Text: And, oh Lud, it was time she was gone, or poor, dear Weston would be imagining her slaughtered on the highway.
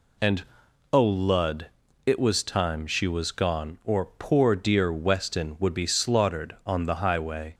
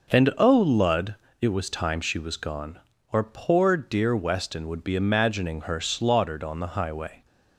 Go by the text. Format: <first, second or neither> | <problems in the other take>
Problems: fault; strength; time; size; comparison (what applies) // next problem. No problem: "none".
second | skips "imagining her"; at 5.8 s